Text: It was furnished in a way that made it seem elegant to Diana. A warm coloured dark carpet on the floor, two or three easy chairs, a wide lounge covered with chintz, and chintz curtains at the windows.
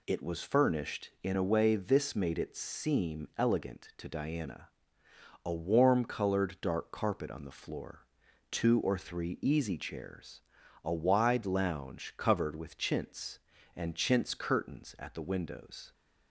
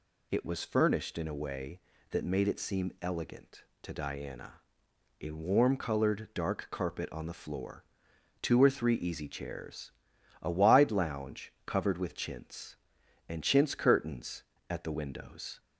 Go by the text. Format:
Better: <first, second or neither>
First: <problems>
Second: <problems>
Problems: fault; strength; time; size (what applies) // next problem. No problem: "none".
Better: second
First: says "this" for "that"; at 1.7 s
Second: none